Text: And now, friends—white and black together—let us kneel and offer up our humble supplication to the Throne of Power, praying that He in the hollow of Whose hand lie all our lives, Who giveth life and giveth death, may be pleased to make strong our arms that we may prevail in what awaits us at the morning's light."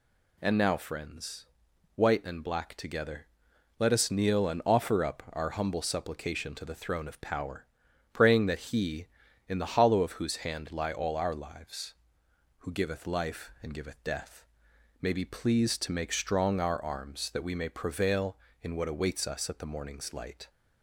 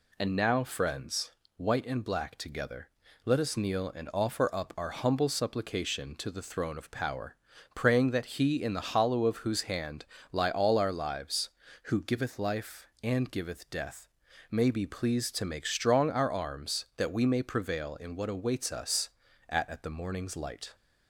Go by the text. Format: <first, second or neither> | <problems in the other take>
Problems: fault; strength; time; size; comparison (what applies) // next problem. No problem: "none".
first | pauses between "hand" and "lie"; slight; at 10.0 s; 0.26 s long // says "at" twice; at 19.6 s